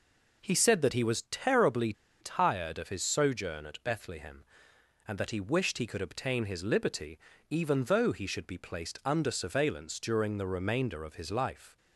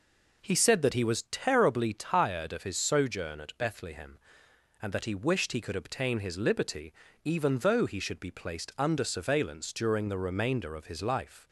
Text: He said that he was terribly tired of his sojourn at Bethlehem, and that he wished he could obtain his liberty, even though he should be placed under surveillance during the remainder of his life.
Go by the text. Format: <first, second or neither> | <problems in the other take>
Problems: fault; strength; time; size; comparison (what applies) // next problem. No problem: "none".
second | pauses between "terribly" and "tired"; slight; at 1.9 s; 0.28 s long